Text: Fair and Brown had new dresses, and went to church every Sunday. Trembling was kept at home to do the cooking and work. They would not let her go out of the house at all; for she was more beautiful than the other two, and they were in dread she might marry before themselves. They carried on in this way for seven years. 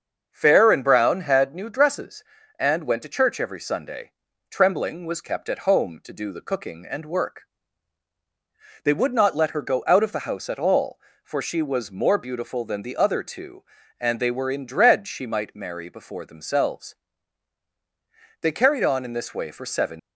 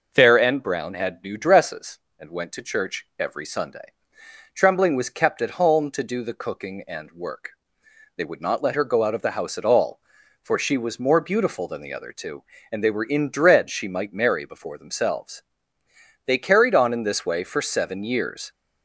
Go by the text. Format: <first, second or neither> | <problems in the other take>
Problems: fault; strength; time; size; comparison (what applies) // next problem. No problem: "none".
second | starts louder than the rest; until 1.3 s; 6.5 dB // stops before "years"; at 19.9 s